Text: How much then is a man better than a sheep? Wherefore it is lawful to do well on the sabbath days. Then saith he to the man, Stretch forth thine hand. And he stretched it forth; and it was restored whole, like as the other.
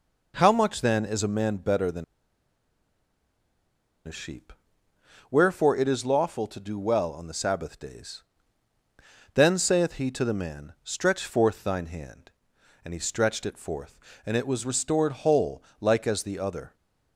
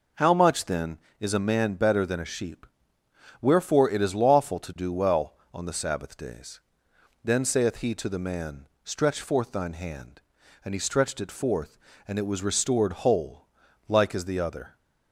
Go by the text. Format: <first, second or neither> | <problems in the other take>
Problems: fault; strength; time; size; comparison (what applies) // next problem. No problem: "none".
second | pauses between "than" and "a"; strong; at 2.0 s; 2.0 s long